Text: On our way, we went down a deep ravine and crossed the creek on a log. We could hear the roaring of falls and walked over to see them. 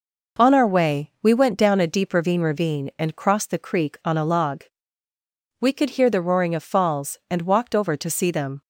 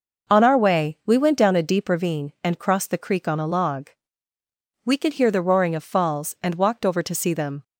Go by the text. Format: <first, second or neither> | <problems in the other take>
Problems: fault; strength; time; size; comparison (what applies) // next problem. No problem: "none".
second | says "ravine" twice; at 2.4 s